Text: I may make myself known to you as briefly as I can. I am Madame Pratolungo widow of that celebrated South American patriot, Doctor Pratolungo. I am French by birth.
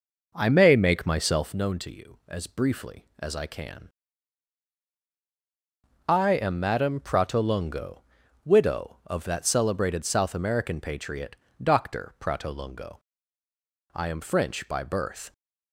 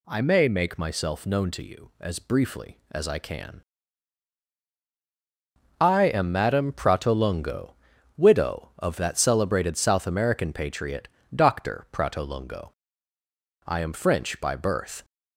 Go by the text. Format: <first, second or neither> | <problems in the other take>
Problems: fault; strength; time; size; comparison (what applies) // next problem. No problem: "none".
second | starts louder than the rest; noticeable; until 1.6 s; 5.5 dB // pauses between "Pratolungo" and "widow"; noticeable; at 7.9 s; 0.46 s long; noticeable in the second